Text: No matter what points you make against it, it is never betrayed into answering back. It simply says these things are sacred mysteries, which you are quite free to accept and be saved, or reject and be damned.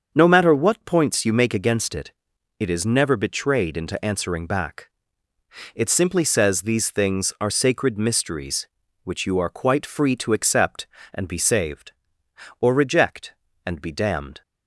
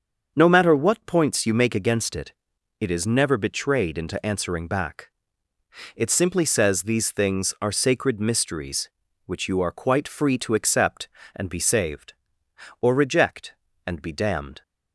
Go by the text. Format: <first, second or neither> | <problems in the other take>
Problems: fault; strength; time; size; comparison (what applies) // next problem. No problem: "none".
neither | starts louder than the rest; the same in both